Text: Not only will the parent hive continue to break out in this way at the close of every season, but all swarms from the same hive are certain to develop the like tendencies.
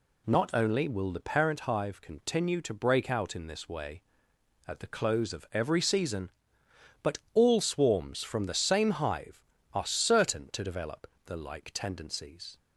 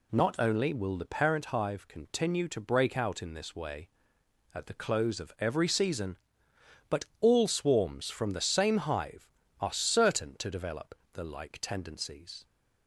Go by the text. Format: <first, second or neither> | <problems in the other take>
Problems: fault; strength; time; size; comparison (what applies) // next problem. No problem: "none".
neither | pauses between "but" and "all"; slight; the same in both // pauses between "develop" and "the"; slight; the same in both